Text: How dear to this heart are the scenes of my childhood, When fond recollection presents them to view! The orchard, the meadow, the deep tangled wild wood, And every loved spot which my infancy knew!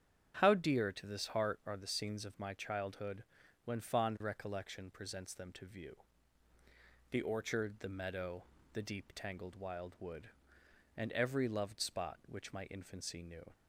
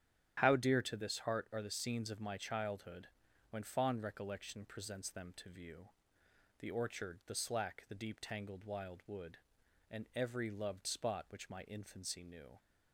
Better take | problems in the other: first | starts louder than the rest; strong; until 1.4 s; 10.5 dB; strong in the first // says "slack" for "meadow"; at 7.3 s

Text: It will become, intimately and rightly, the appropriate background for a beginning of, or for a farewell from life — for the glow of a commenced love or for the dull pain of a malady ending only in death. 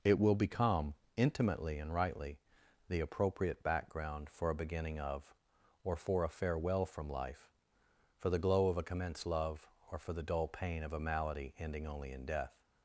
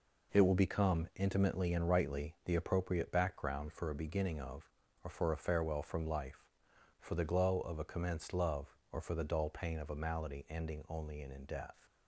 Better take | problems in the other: first | says "in" twice; at 11.3 s

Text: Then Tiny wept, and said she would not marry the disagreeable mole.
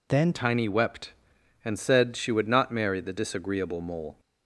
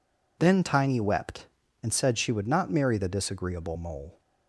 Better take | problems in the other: second | changes voice at "Tiny"; from 0.3 s on; 3.8 s long

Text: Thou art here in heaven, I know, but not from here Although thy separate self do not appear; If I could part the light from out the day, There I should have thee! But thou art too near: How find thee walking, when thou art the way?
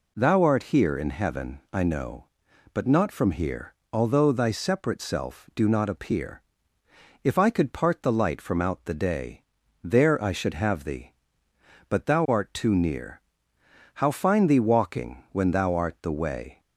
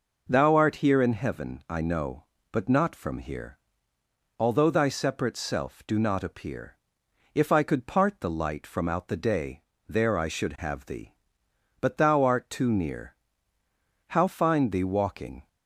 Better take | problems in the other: first | pauses between "here" and "Although"; noticeable; at 3.5 s; 0.82 s long; slight in the first // stops before "when thou art the way"; at 15.4 s

